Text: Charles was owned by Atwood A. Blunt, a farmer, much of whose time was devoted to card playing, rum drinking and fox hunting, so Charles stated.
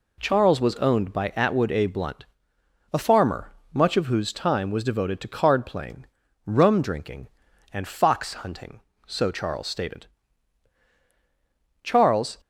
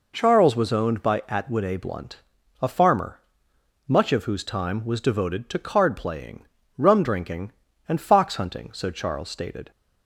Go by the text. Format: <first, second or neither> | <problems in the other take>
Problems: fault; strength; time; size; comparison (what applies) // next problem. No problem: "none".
second | goes on to say "Charles"; from 11.8 s on; 0.56 s long